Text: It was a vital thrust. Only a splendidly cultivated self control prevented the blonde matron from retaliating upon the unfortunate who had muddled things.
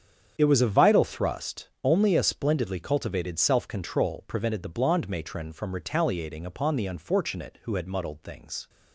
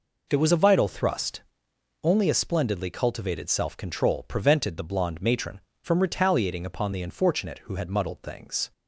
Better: second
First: gets quieter; strong; throughout; 12.5 dB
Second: none

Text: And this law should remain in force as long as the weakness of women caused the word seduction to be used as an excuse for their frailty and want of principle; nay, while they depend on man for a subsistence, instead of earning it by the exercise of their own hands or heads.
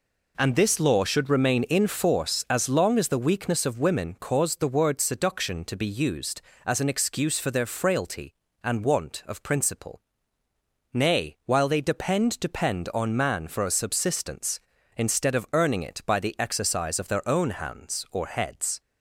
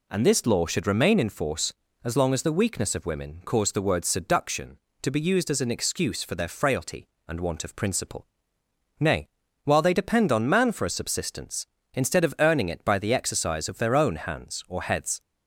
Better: second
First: says "depend" twice; at 12.4 s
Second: none

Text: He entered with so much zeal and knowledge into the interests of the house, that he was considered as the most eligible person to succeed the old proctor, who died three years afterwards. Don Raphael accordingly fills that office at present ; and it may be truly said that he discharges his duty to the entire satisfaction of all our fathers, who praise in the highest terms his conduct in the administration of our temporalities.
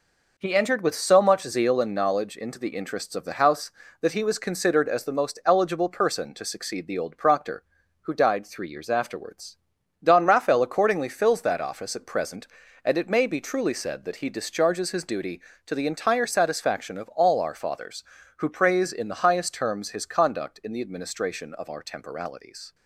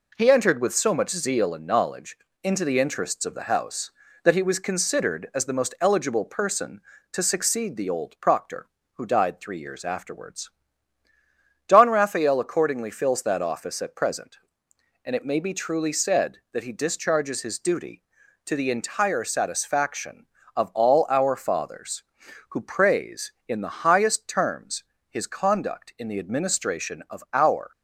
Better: first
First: none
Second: pauses between "knowledge" and "into"; slight; at 2.1 s; 0.26 s long // pauses between "terms" and "his"; slight; at 24.8 s; 0.26 s long // stops before "temporalities"; at 27.7 s

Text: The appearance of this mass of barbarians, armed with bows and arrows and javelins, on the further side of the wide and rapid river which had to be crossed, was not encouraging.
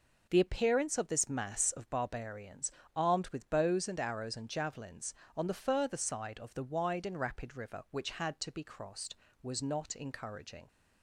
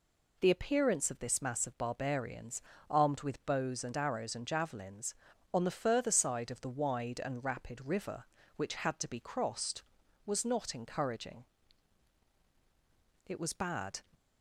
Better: first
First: none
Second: goes on to say "It was bad"; noticeable; from 13.2 s on; 0.76 s long

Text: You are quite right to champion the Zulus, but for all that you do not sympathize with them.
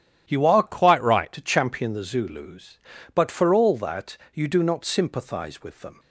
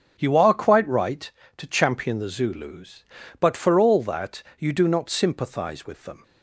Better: second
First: starts louder than the rest; strong; until 1.2 s; 10 dB // changes voice from "quite" to "right"; from 0.6 to 1.3 s; 0.7 s long // pauses between "that" and "you"; slight; at 4.1 s; 0.18 s long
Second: starts louder than the rest; strong; until 1.1 s; 7 dB // pauses between "that" and "you"; slight; at 4.4 s; 0.17 s long

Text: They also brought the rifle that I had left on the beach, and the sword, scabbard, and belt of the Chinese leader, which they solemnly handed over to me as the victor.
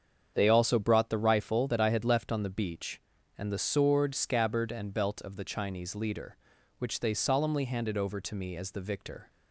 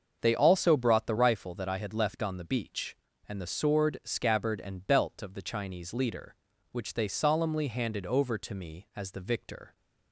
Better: neither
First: starts louder than the rest; strong; until 1.3 s; 7.5 dB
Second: starts louder than the rest; until 1.2 s; 6.5 dB

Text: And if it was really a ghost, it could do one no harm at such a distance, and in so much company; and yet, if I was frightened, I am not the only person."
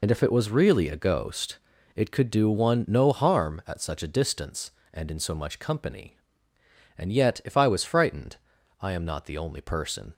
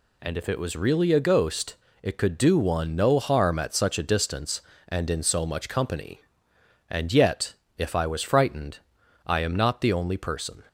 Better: second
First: loses the start of "And"; at 0.0 s; 35 ms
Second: none

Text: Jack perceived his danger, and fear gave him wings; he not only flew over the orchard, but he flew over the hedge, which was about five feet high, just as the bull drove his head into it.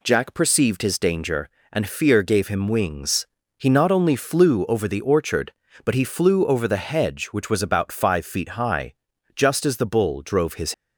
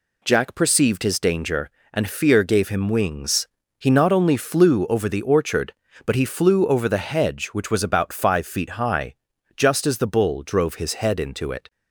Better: second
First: stops before "head into it"; at 10.7 s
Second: none

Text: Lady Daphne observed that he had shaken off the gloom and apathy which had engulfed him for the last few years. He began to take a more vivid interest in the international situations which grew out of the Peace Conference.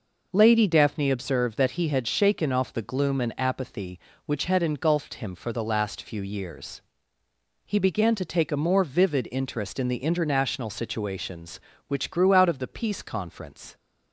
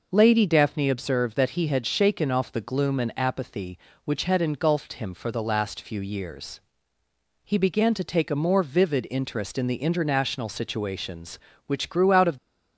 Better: first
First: none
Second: stops before "the Peace Conference"; at 12.3 s

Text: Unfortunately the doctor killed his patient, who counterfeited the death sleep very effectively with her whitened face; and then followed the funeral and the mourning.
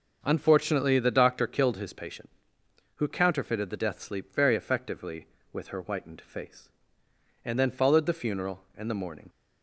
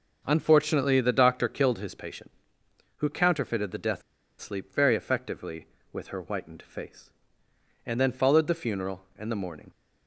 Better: first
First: starts louder than the rest; noticeable; until 1.2 s; 6 dB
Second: starts louder than the rest; until 1.2 s; 6.5 dB // pauses between "death" and "sleep"; at 4.0 s; 0.37 s long

